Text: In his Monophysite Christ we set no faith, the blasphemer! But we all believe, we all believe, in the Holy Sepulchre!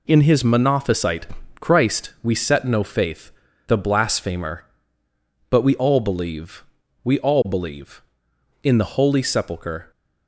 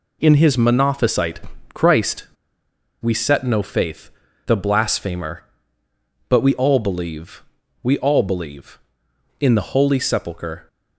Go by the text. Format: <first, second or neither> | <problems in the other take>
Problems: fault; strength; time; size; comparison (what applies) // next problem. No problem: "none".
first | pauses between "Monophysite" and "Christ"; slight; at 1.3 s; 0.32 s long; slight in the first // pauses between "Christ" and "we"; noticeable; at 2.2 s; 0.75 s long